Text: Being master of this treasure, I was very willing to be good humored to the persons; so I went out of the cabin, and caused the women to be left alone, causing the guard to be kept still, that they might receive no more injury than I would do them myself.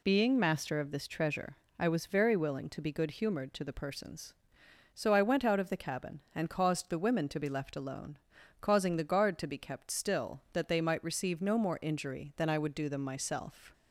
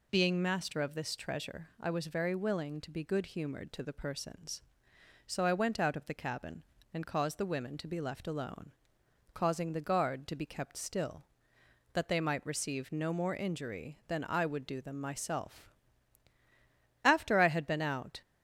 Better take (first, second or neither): first